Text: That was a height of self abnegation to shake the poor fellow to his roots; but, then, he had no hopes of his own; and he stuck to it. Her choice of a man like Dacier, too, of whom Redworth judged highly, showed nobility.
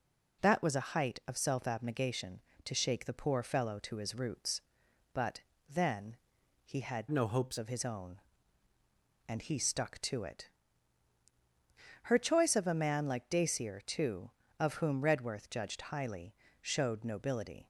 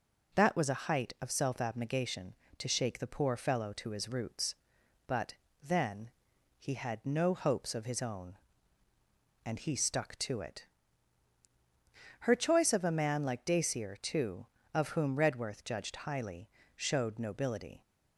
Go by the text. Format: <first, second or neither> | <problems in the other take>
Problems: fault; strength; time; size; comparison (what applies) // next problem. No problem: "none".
second | changes voice from "no" to "hopes"; from 7.0 to 7.5 s; 0.5 s long